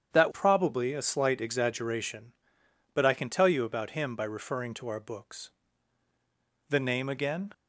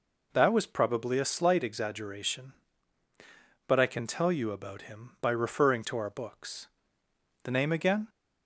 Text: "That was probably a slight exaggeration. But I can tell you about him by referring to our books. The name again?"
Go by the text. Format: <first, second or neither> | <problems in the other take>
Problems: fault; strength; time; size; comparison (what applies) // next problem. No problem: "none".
second | starts louder than the rest; strong; until 1.1 s; 8.5 dB // skips "was"; at 0.3 s